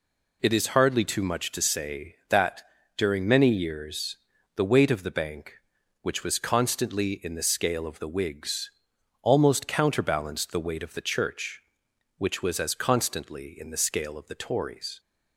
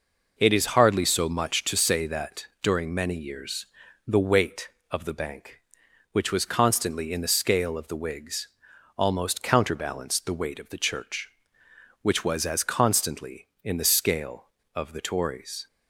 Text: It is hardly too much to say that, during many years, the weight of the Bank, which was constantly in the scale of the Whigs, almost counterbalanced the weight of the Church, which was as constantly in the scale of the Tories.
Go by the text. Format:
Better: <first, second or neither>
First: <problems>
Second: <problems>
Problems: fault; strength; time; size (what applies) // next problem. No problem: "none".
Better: first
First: none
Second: says "so" for "too"; at 1.0 s